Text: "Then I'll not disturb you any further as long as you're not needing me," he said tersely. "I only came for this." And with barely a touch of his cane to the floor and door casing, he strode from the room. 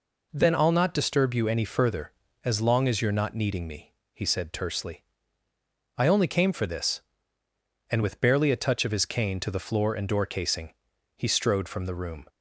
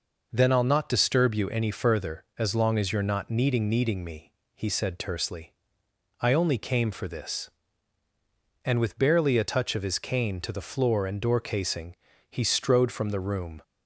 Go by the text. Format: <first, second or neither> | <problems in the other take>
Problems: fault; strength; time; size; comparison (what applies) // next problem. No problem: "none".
first | says "needing" twice; at 3.6 s